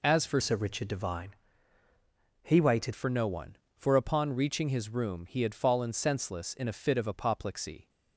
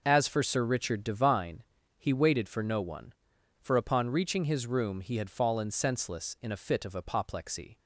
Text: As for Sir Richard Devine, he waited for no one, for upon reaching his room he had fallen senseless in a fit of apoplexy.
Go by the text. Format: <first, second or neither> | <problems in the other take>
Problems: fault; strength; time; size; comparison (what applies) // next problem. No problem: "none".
second | changes voice from "Sir" to "waited"; from 0.4 to 2.9 s; 2.5 s long